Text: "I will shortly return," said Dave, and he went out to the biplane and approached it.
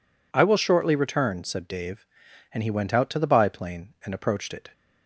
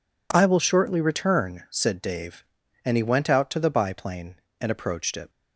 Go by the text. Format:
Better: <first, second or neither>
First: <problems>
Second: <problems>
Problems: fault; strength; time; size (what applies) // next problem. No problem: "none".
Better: neither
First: none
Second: none